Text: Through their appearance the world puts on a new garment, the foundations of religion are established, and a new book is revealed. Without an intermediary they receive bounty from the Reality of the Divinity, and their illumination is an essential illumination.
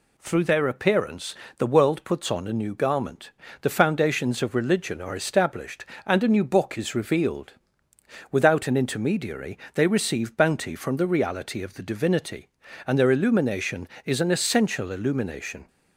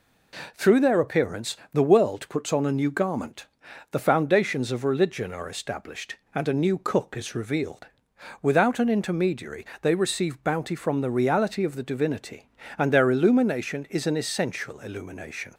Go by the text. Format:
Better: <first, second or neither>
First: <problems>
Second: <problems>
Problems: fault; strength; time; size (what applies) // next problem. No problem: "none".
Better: first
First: pauses between "appearance" and "the"; slight; at 1.3 s; 0.22 s long // pauses between "intermediary" and "they"; slight; at 9.5 s; 0.18 s long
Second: pauses between "appearance" and "the"; slight; at 1.5 s; 0.16 s long // says "cook" for "book"; at 6.7 s // pauses between "intermediary" and "they"; slight; at 9.6 s; 0.18 s long